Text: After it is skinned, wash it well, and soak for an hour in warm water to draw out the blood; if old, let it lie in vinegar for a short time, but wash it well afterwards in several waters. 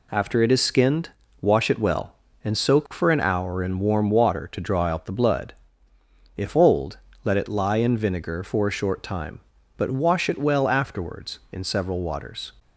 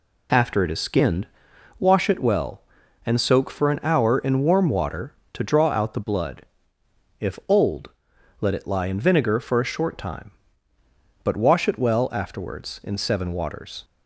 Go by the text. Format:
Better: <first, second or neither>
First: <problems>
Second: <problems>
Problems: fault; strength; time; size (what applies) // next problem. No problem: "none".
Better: first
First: none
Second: says "seven" for "several"; at 12.9 s